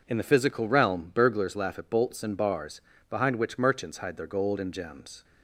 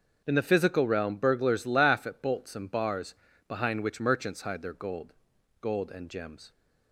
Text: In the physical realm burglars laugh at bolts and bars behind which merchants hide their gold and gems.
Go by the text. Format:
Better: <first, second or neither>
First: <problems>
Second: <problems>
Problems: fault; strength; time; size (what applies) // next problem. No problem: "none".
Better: first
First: pauses between "bars" and "behind"; slight; at 2.8 s; 0.28 s long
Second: starts louder than the rest; noticeable; until 1.2 s; 6 dB // pauses between "bars" and "behind"; slight; at 3.1 s; 0.36 s long // says "gold" twice; at 5.6 s